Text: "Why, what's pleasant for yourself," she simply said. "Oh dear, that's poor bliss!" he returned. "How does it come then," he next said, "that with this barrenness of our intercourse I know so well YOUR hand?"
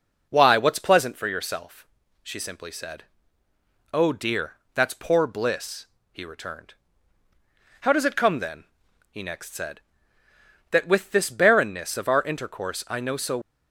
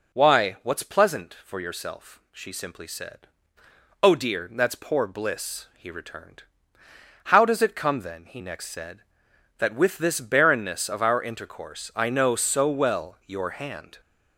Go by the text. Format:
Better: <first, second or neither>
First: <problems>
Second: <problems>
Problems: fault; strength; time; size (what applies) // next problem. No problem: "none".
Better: second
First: stops before "well YOUR hand"; at 13.4 s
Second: none